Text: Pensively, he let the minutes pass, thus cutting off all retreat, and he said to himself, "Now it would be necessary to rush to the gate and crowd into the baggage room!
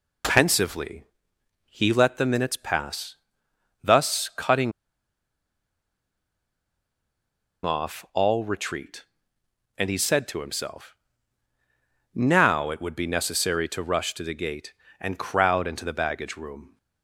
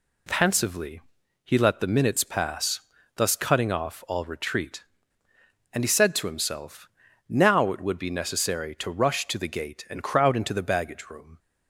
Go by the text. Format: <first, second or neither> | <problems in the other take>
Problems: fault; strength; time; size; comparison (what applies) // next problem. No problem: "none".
second | pauses between "cutting" and "off"; strong; at 4.7 s; 2.9 s long